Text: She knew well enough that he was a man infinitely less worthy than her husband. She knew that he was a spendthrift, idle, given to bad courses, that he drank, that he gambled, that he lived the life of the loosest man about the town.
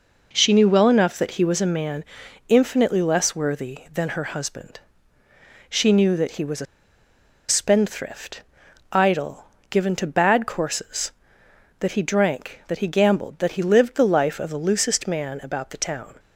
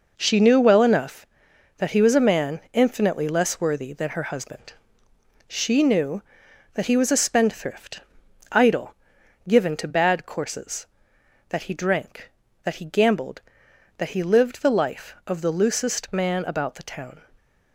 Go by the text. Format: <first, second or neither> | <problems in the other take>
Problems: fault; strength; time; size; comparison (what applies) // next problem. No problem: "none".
second | pauses between "man" and "infinitely"; at 2.0 s; 0.44 s long // pauses between "a" and "spendthrift"; noticeable; at 6.6 s; 0.83 s long